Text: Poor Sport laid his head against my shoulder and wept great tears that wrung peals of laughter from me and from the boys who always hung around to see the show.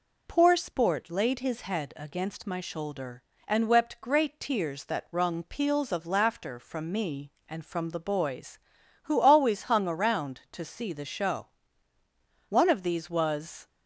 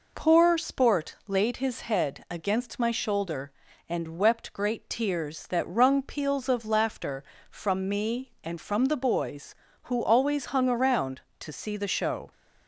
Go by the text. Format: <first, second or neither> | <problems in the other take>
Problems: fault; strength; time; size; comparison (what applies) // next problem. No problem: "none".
second | goes on to say "One of these was"; noticeable; from 12.4 s on; 1.1 s long